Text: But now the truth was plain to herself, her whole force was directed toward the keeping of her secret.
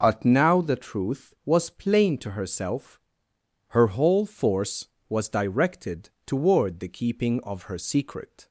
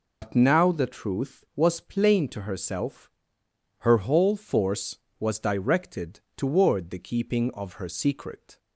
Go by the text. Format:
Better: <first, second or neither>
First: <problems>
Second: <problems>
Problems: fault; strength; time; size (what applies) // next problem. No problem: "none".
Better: first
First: pauses between "directed" and "toward"; slight; at 6.0 s; 0.16 s long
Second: loses the start of "But"; at 0.2 s; 110 ms // pauses between "directed" and "toward"; slight; at 6.1 s; 0.16 s long